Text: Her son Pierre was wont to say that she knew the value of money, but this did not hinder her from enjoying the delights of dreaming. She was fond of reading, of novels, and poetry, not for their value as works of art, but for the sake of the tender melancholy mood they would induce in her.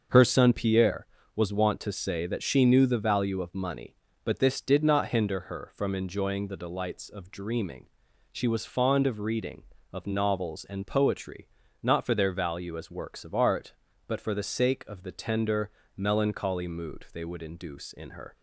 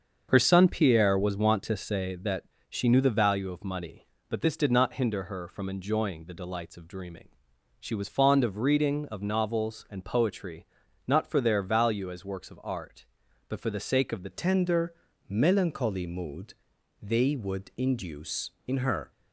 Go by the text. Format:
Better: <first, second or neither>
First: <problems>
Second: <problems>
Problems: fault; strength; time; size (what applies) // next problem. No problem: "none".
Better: first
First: starts louder than the rest; until 1.4 s; 6.5 dB // pauses between "tender" and "melancholy"; slight; at 15.6 s; 0.26 s long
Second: starts louder than the rest; until 1.3 s; 7 dB // pauses between "that" and "she"; slight; at 2.4 s; 0.26 s long // changes voice at "tender"; from 14.3 s on; 4.8 s long // pauses between "tender" and "melancholy"; slight; at 14.9 s; 0.34 s long // pauses between "mood" and "they"; noticeable; at 16.5 s; 0.48 s long